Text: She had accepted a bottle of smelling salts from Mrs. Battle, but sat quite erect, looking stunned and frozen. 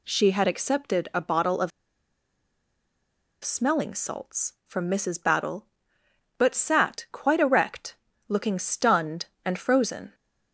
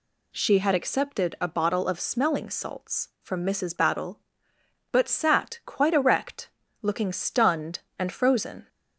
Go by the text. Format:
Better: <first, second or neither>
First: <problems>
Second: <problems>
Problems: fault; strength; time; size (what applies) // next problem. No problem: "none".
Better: second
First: pauses between "of" and "smelling"; strong; at 1.7 s; 1.7 s long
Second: none